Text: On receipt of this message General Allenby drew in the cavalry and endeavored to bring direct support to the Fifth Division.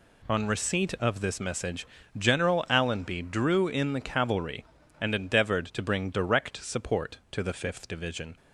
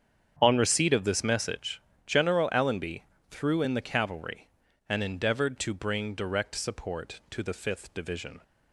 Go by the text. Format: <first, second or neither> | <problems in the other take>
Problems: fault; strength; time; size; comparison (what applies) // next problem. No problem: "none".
first | starts louder than the rest; strong; until 1.4 s; 8.5 dB // pauses between "message" and "General"; slight; at 1.8 s; 0.24 s long; slight in the first // says "threw" for "drew"; at 3.3 s